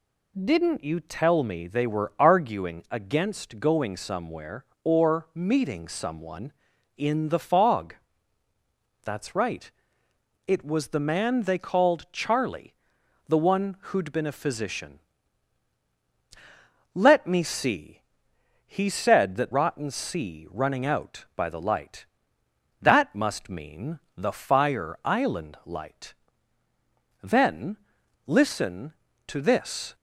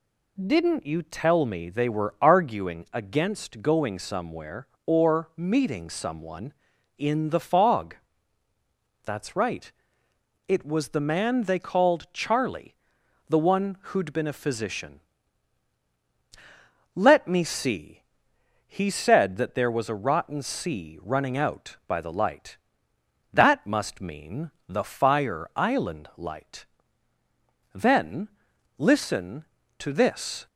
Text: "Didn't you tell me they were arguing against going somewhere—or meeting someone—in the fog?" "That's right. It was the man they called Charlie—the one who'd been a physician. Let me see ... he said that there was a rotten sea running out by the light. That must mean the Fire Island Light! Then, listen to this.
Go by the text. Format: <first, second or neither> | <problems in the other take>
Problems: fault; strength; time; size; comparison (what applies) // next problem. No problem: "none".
second | skips "there was a"; at 19.5 s // pauses between "mean" and "the"; slight; at 23.9 s; 0.16 s long; slight in the second